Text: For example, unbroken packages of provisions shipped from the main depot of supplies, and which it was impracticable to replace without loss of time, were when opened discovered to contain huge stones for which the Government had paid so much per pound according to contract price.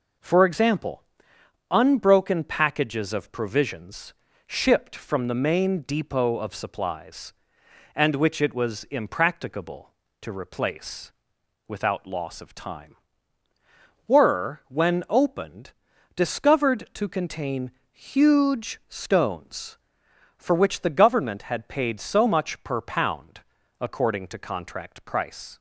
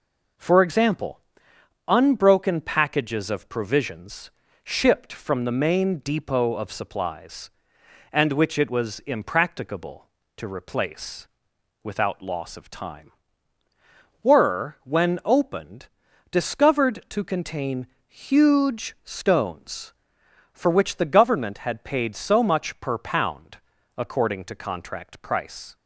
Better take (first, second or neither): neither